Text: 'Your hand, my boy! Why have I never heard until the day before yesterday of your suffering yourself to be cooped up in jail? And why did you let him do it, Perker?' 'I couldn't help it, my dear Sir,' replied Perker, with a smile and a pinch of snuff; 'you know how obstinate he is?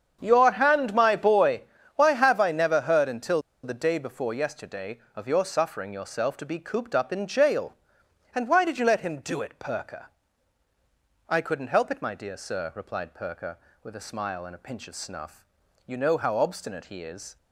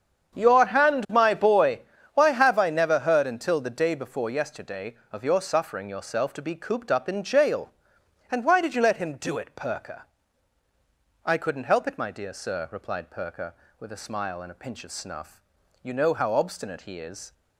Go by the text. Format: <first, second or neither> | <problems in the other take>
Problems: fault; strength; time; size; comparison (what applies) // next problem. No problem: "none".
second | starts louder than the rest; strong; until 1.2 s; 7.5 dB; strong in the second // pauses between "until" and "the"; slight; at 3.4 s; 0.22 s long